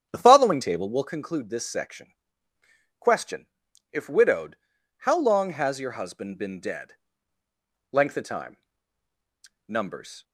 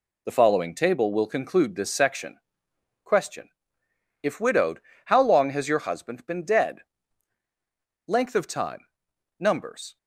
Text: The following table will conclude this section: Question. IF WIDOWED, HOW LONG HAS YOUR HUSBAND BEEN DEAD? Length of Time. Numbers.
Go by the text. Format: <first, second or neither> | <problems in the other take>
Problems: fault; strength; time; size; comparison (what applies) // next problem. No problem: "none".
second | starts louder than the rest; strong; until 1.1 s; 9 dB